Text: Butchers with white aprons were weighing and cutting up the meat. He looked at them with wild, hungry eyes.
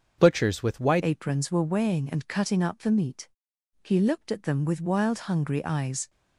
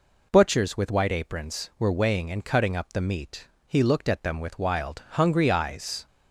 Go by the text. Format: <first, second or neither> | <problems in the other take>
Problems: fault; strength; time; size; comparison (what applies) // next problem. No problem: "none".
second | starts louder than the rest; until 1.2 s; 7 dB // changes voice at "aprons"; from 1.0 s on; 5.0 s long